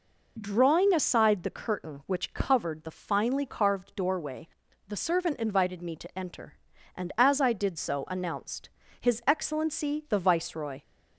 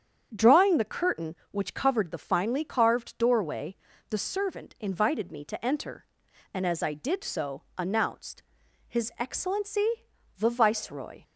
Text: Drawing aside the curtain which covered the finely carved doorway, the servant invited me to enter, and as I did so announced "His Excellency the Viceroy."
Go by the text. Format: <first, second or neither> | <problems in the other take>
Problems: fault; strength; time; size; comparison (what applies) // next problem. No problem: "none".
first | starts louder than the rest; strong; until 1.3 s; 8 dB // skips "aside"; at 0.7 s // pauses between "announced" and "His"; noticeable; at 8.4 s; 0.46 s long; slight in the first // pauses between "Excellency" and "the"; noticeable; at 9.8 s; 0.50 s long